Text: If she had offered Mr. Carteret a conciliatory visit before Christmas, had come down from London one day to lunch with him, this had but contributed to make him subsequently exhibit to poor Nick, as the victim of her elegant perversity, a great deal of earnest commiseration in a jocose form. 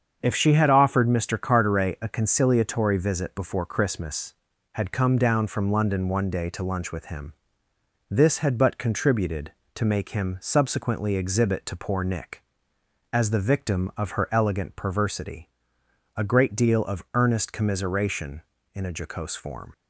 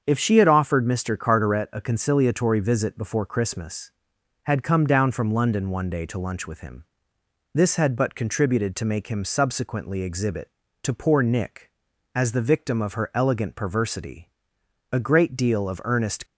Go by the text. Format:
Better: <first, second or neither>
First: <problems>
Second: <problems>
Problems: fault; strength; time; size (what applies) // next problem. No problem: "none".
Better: first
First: starts louder than the rest; strong; until 1.2 s; 7 dB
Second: starts louder than the rest; until 1.0 s; 7 dB // stops before "commiseration in a jocose form"; at 16.2 s